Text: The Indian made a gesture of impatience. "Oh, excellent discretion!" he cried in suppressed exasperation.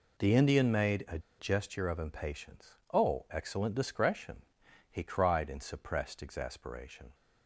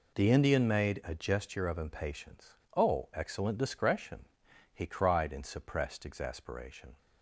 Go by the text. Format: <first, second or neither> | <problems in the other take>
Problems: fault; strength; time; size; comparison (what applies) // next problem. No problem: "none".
second | pauses between "a" and "gesture"; slight; at 1.1 s; 0.19 s long